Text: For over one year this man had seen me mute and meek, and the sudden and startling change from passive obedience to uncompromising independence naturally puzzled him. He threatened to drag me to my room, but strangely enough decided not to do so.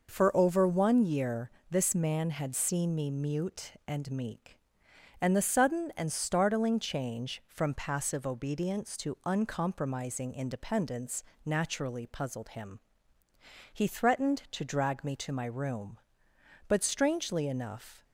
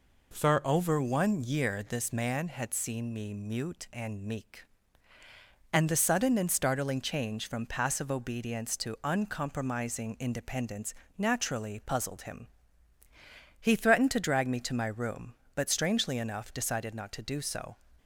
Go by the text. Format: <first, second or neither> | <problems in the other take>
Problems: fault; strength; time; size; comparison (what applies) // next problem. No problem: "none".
second | pauses between "year" and "this"; slight; at 1.5 s; 0.18 s long // pauses between "independence" and "naturally"; slight; at 11.2 s; 0.24 s long; slight in the second // stops before "decided not to do so"; at 18.0 s